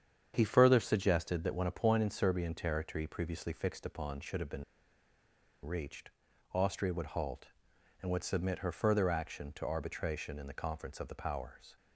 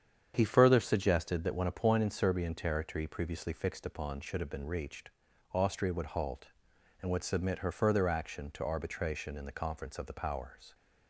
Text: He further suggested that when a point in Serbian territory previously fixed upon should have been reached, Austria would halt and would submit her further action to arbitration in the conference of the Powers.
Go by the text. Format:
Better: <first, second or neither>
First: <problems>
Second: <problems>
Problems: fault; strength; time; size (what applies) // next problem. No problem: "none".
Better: second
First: starts louder than the rest; strong; until 1.3 s; 8 dB // pauses between "been" and "reached"; at 4.6 s; 1.0 s long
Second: starts louder than the rest; strong; until 1.3 s; 8 dB